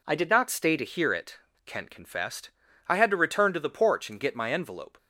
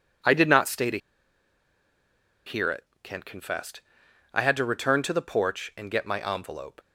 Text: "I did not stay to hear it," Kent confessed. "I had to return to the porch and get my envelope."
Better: first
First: none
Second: pauses between "to" and "hear"; strong; at 0.9 s; 1.4 s long

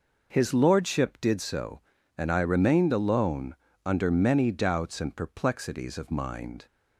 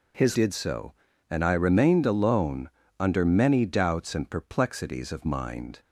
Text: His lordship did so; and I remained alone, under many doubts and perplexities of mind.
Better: first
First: none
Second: skips "lordship"; at 0.3 s

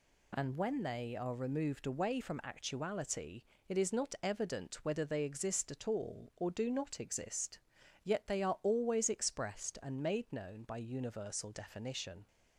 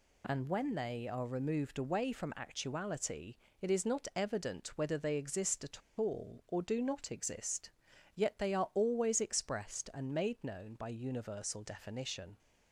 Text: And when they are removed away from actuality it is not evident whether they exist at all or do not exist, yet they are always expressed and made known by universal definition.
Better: first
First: pauses between "actuality" and "it"; slight; at 3.4 s; 0.26 s long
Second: pauses between "actuality" and "it"; slight; at 3.3 s; 0.26 s long // pauses between "at" and "all"; slight; at 5.8 s; 0.19 s long

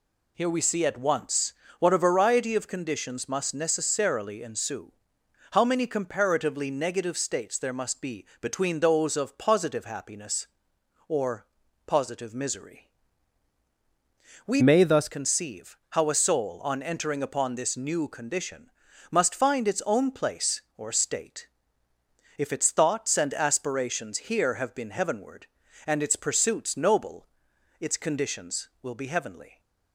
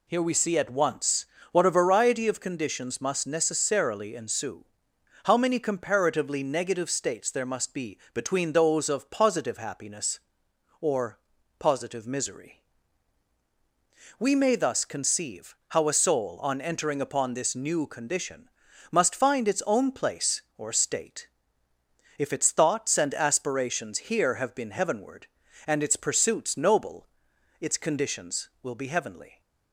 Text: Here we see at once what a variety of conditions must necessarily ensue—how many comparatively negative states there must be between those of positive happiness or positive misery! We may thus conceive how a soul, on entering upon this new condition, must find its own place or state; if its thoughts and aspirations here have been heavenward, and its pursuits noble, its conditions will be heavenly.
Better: second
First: pauses between "once" and "what"; slight; at 1.5 s; 0.26 s long // pauses between "be" and "between"; slight; at 8.2 s; 0.16 s long // pauses between "or" and "positive"; at 11.4 s; 0.40 s long // changes voice from "may" to "thus"; from 14.6 to 15.0 s; 0.4 s long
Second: pauses between "once" and "what"; slight; at 1.2 s; 0.26 s long // pauses between "be" and "between"; slight; at 7.9 s; 0.16 s long // pauses between "or" and "positive"; at 11.1 s; 0.40 s long

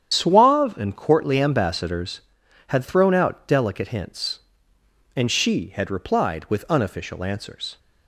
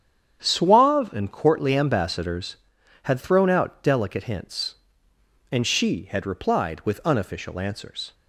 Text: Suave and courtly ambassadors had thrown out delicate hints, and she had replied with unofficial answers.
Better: second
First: loses the start of "Suave"; at 0.1 s; 55 ms // starts louder than the rest; strong; until 1.1 s; 9 dB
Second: starts louder than the rest; strong; until 1.4 s; 8 dB

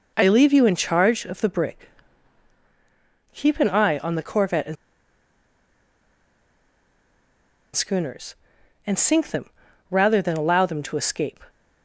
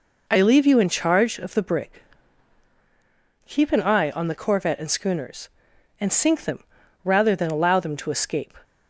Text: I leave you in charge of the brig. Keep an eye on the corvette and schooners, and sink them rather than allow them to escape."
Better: second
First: pauses between "and" and "schooners"; strong; at 4.7 s; 2.9 s long // pauses between "them" and "rather"; at 9.4 s; 0.40 s long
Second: pauses between "them" and "rather"; at 6.6 s; 0.40 s long

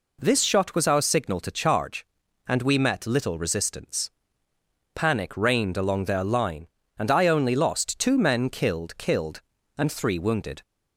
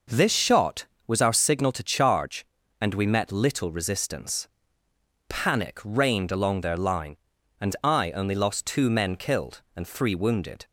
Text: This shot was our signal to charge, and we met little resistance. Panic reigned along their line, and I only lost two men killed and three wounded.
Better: second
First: says "killed" twice; at 8.9 s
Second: none

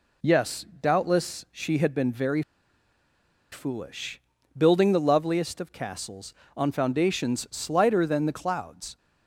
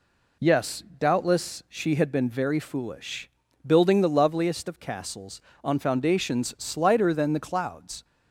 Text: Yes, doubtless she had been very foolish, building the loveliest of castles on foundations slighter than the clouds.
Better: second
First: pauses between "very" and "foolish"; at 2.4 s; 1.0 s long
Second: none

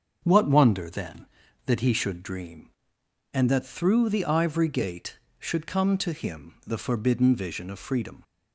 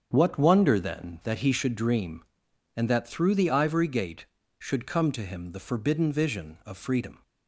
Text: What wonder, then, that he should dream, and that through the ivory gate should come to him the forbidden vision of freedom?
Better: neither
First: starts louder than the rest; until 1.2 s; 6.5 dB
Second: starts louder than the rest; strong; until 1.1 s; 7 dB

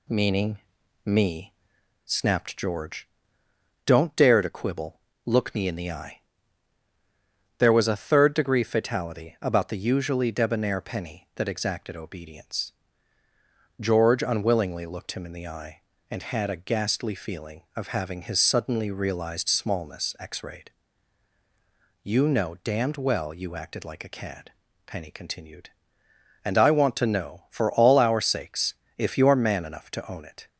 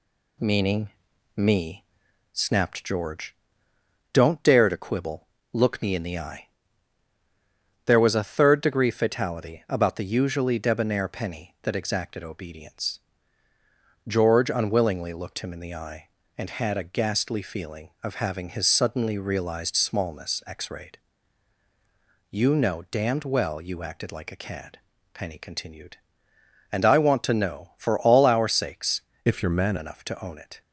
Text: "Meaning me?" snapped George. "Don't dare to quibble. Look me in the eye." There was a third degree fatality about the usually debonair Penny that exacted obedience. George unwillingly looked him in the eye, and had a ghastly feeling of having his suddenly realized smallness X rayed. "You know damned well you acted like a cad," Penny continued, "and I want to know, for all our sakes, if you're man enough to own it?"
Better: first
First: pauses between "Meaning" and "me"; noticeable; at 0.5 s; 0.46 s long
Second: pauses between "Meaning" and "me"; noticeable; at 0.8 s; 0.46 s long // changes voice from "if" to "man"; from 29.2 to 29.7 s; 0.5 s long

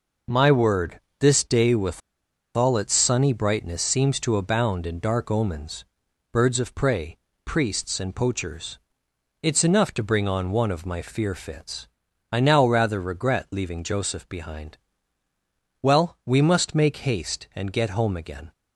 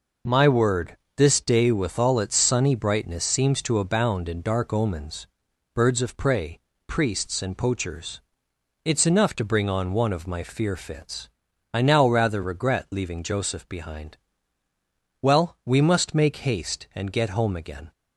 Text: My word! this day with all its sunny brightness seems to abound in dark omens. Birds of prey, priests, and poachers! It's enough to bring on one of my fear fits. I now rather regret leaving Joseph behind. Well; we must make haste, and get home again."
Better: second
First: pauses between "with" and "all"; noticeable; at 2.0 s; 0.57 s long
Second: none

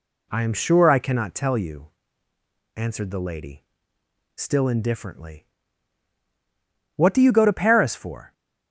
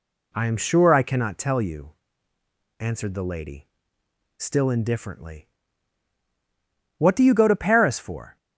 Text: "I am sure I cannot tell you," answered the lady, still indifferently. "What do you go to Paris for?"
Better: neither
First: none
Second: none

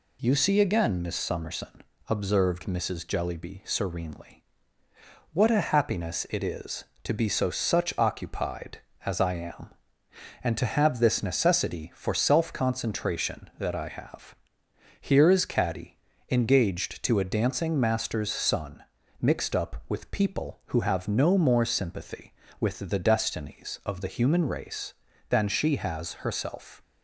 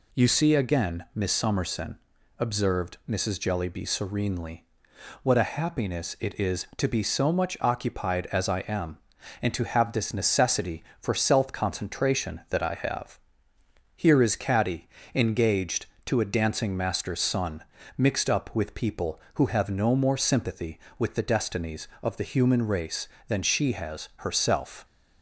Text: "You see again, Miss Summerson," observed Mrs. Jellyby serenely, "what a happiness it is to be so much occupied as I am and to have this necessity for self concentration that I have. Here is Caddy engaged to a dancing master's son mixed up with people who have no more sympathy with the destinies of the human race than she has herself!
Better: second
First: says "such" for "much"; at 7.4 s // pauses between "Caddy" and "engaged"; slight; at 15.9 s; 0.32 s long // pauses between "son" and "mixed"; at 18.8 s; 0.40 s long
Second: pauses between "Caddy" and "engaged"; slight; at 14.8 s; 0.26 s long // pauses between "son" and "mixed"; slight; at 17.6 s; 0.34 s long

